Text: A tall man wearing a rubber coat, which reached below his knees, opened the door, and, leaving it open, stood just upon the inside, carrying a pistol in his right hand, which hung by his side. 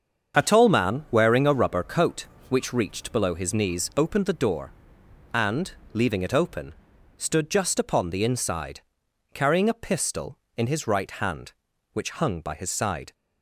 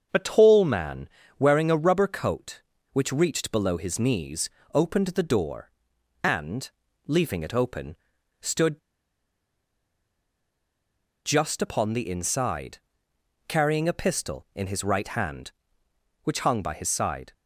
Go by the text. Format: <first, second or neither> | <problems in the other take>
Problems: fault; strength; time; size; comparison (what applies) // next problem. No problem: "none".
first | starts louder than the rest; until 1.4 s; 7 dB; also in the first // pauses between "man" and "wearing"; slight; at 1.0 s; 0.30 s long // pauses between "stood" and "just"; strong; at 8.7 s; 2.4 s long